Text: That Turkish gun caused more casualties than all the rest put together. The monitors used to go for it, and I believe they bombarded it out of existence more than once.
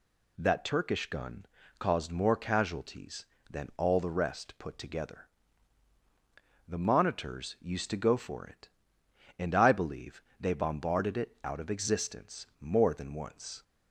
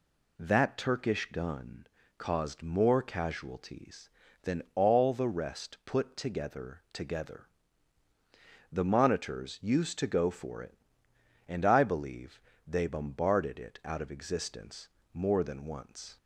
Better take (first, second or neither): first